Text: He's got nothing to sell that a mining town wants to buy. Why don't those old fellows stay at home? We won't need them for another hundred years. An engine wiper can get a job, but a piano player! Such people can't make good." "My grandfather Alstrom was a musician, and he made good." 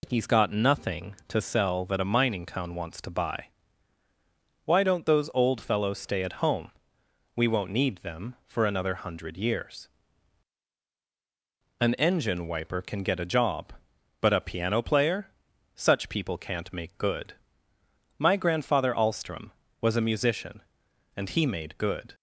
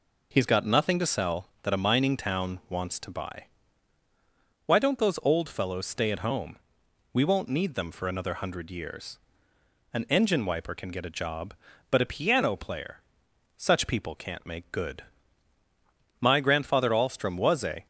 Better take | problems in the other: first | stops before "musician and he made good"; at 17.8 s

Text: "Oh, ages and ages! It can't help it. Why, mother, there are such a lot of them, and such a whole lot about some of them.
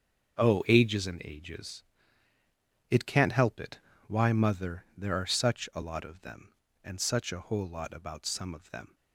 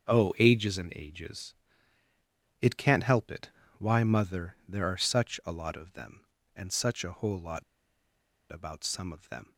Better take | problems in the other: first | starts louder than the rest; until 1.1 s; 6.5 dB; also in the first // pauses between "lot" and "about"; noticeable; at 7.6 s; 0.88 s long

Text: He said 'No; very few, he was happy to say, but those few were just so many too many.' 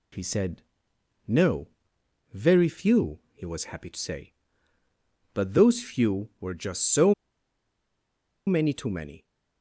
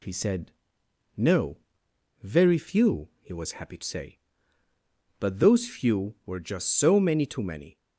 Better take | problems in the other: second | pauses between "said" and "No"; noticeable; at 0.6 s; 0.64 s long; noticeable in the second // pauses between "so" and "many"; strong; at 7.1 s; 1.3 s long

